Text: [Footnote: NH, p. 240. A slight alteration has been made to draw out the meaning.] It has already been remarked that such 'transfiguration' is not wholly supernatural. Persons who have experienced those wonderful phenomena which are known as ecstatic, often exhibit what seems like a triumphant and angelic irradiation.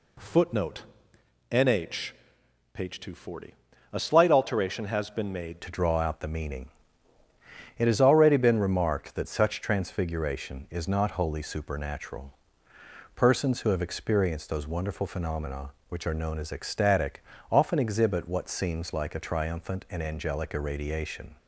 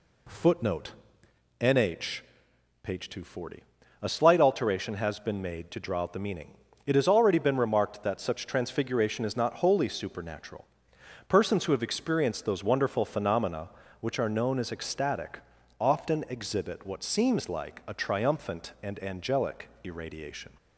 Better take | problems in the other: second | changes voice at "to"; from 5.6 s on; 15.7 s long

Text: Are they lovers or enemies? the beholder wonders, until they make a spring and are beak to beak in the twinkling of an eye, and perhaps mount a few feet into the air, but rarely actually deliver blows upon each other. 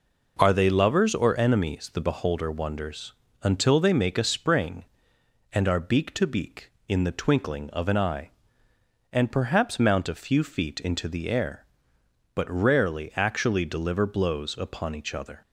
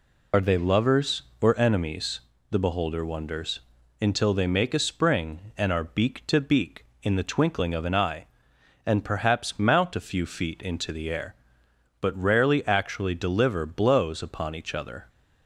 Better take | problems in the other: first | loses the start of "Are"; at 0.3 s; 55 ms

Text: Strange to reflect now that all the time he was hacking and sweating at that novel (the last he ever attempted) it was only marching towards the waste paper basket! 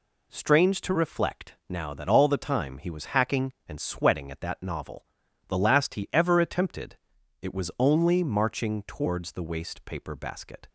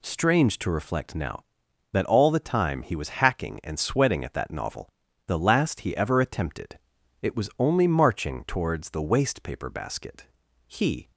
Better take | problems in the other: first | goes on to say "He"; slight; from 10.6 s on; 0.44 s long

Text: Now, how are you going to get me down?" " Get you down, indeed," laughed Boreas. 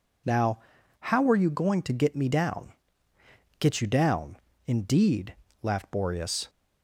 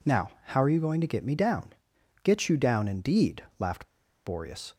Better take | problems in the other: first | pauses between "laughed" and "Boreas"; at 3.8 s; 0.38 s long

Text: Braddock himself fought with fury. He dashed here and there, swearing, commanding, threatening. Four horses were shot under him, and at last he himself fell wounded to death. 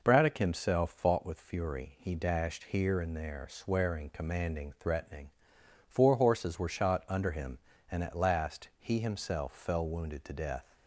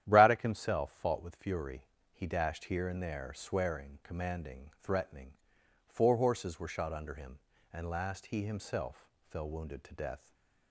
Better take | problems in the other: first | starts louder than the rest; strong; until 1.0 s; 11 dB // skips "at"; at 7.8 s // pauses between "himself" and "fell"; slight; at 9.0 s; 0.22 s long // stays silent after the last word; slight; from 10.1 s on; 0.6 s long

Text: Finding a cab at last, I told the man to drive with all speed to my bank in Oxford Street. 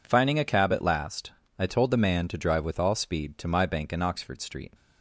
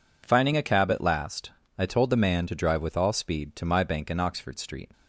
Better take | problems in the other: neither | none

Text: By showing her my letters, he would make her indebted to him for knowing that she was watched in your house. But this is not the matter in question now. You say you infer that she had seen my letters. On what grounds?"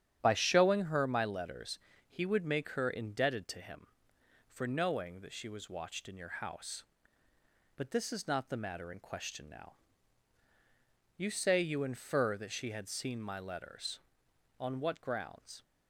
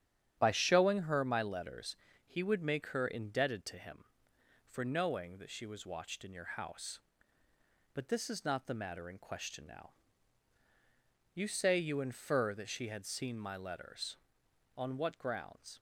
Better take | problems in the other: neither | starts louder than the rest; strong; the same in both

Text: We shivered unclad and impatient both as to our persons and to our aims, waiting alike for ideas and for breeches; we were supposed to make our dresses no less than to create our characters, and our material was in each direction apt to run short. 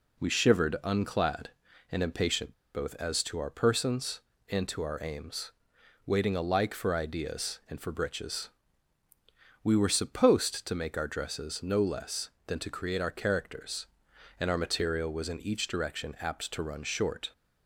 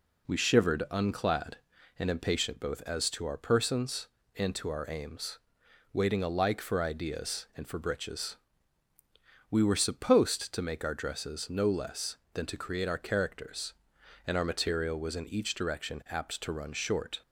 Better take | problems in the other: second | pauses between "impatient" and "both"; slight; at 2.5 s; 0.22 s long

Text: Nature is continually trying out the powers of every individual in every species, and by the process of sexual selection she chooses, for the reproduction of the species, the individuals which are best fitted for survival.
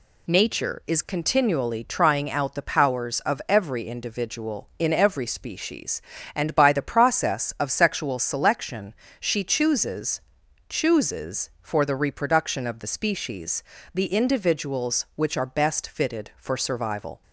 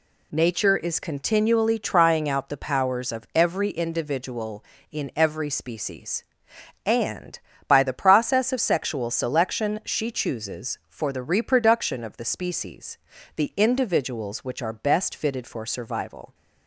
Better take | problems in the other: second | pauses between "selection" and "she"; slight; at 8.9 s; 0.28 s long // says "chooses" twice; at 10.6 s

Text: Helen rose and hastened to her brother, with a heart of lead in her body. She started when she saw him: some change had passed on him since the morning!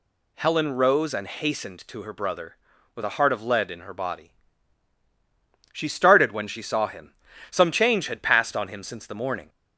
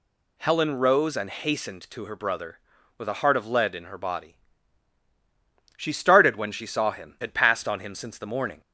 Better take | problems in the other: first | skips "some change"; at 7.1 s

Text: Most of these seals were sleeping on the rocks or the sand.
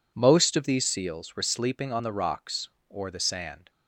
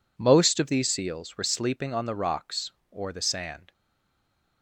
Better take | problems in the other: first | stays silent after the last word; slight; from 3.7 s on; 0.9 s long

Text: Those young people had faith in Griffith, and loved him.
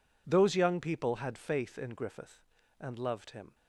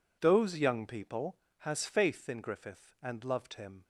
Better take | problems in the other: first | says "has" for "had"; at 1.5 s

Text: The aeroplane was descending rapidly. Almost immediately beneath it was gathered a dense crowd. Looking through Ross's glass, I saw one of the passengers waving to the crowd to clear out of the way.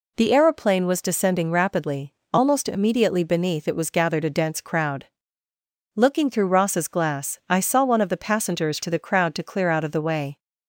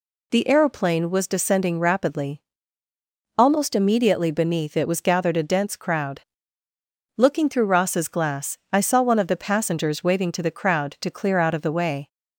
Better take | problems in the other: second | skips "waving"; at 8.8 s

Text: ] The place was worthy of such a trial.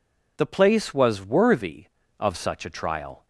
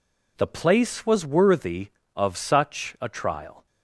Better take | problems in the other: neither | none

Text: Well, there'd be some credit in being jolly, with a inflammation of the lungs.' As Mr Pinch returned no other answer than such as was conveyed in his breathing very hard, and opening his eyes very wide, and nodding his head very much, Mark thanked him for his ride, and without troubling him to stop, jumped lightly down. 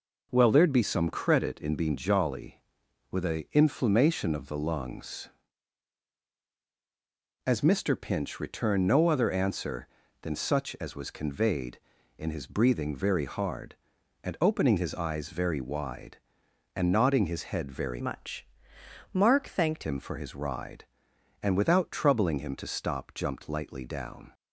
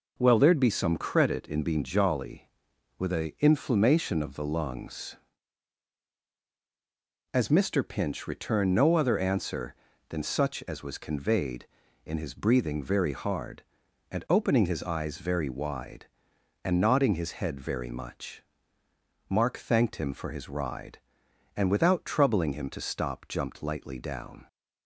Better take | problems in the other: second | changes voice from "much" to "thanked"; from 17.9 to 19.8 s; 1.9 s long

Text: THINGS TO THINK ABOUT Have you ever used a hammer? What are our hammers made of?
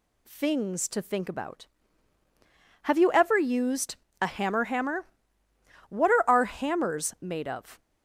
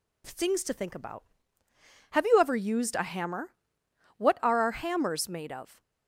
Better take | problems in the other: second | pauses between "used" and "a"; slight; at 3.9 s; 0.24 s long // says "hammer" twice; at 4.6 s

